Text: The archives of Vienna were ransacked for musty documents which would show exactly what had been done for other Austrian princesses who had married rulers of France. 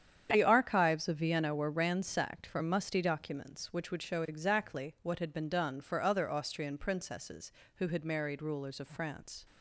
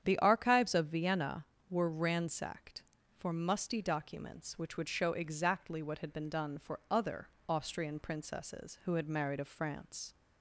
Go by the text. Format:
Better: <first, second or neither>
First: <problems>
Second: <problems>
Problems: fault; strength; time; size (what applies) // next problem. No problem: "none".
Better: first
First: starts louder than the rest; strong; until 1.3 s; 8.5 dB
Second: starts louder than the rest; strong; until 1.0 s; 9 dB // pauses between "other" and "Austrian"; slight; at 7.2 s; 0.20 s long // skips "rulers"; at 9.3 s